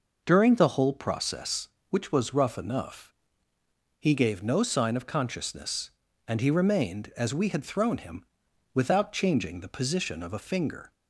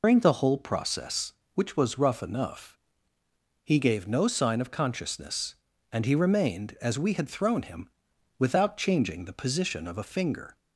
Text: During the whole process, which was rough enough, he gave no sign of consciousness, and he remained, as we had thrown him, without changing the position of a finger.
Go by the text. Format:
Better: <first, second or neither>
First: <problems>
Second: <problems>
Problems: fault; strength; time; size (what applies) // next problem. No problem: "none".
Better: first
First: none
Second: loses the start of "During"; at 0.0 s; 145 ms